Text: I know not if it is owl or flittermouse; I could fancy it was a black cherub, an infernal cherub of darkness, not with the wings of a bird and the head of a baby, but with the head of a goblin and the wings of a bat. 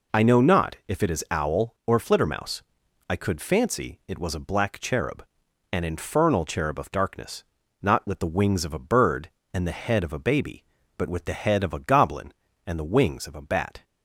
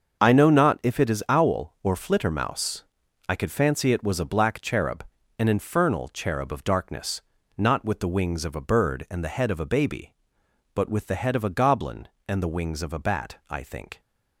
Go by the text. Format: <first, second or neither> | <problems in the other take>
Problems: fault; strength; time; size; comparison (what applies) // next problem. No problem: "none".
first | starts louder than the rest; until 1.2 s; 6.5 dB // goes on to say "I think"; from 13.4 s on; 0.52 s long